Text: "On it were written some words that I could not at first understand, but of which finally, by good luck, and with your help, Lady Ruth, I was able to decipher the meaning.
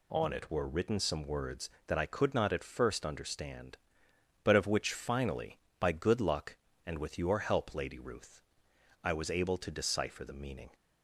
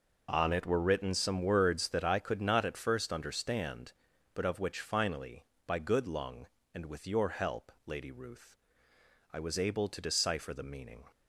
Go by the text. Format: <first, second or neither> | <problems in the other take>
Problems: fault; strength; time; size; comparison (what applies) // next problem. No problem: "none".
first | says "lung" for "luck"; at 6.0 s